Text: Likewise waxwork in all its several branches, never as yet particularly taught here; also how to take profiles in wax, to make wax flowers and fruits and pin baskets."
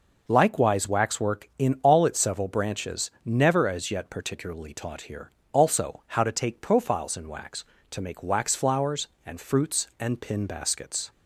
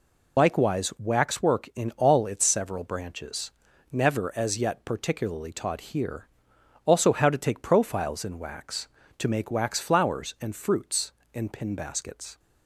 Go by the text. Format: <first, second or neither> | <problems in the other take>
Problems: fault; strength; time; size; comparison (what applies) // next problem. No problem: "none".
first | loses the start of "Likewise"; at 0.3 s; 40 ms